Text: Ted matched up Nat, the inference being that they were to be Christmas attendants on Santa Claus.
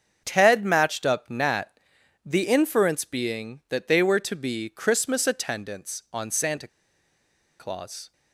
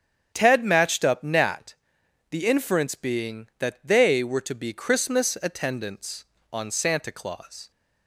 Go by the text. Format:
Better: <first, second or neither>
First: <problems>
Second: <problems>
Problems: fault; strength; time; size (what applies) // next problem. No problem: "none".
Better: second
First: starts louder than the rest; strong; until 1.2 s; 7 dB // pauses between "Santa" and "Claus"; noticeable; at 6.6 s; 0.91 s long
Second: starts louder than the rest; strong; until 1.3 s; 8 dB